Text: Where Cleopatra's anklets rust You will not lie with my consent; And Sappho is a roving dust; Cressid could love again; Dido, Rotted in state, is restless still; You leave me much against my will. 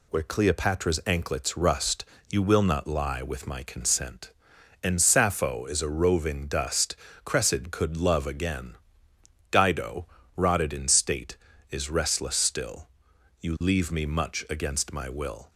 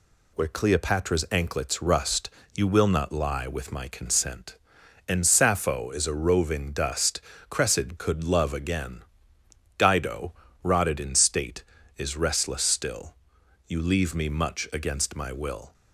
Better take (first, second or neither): neither